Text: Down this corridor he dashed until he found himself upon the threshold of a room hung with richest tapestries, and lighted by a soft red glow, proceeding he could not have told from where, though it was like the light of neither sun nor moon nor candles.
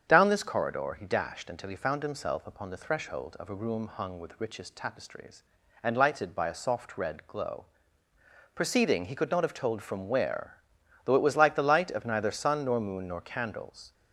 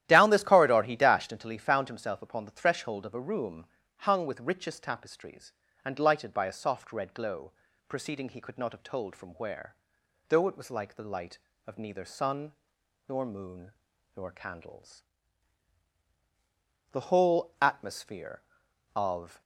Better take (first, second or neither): first